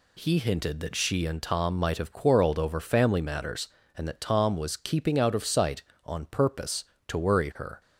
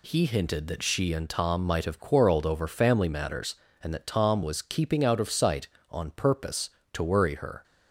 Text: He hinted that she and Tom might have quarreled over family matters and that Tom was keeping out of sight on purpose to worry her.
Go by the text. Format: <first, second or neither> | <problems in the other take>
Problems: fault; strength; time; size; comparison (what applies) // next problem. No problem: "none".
neither | none